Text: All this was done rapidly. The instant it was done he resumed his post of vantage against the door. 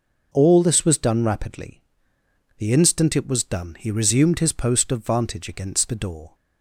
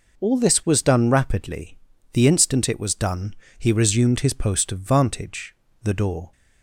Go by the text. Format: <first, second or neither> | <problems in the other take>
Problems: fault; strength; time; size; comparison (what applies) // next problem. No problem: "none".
first | pauses between "done" and "he"; slight; at 3.3 s; 0.22 s long // skips "against"; at 5.6 s